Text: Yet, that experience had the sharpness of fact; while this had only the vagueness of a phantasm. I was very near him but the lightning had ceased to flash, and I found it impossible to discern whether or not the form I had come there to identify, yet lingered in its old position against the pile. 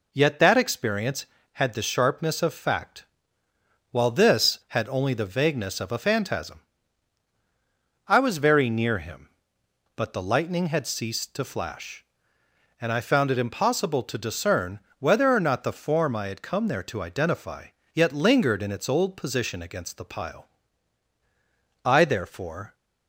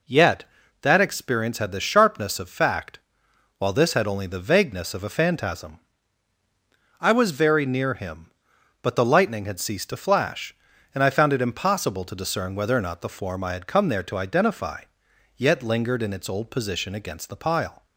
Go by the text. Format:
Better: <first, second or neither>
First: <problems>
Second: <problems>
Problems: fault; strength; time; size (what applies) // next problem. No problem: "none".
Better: second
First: pauses between "discern" and "whether"; slight; at 14.7 s; 0.22 s long // goes on to say "I therefore"; noticeable; from 21.8 s on; 0.90 s long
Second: none